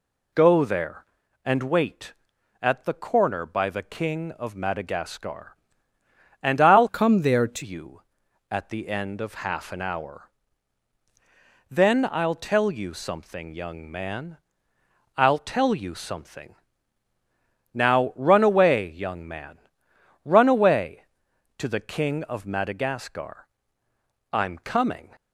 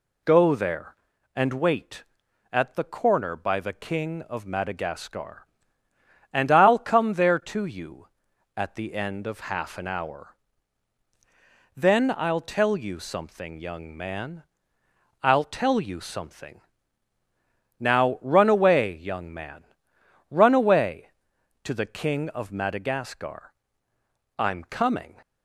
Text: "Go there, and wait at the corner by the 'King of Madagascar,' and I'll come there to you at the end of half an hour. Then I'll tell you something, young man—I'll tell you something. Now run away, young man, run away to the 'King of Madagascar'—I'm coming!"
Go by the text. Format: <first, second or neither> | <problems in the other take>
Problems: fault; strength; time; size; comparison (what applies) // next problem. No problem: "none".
second | changes voice from "come" to "to"; from 6.8 to 7.6 s; 0.8 s long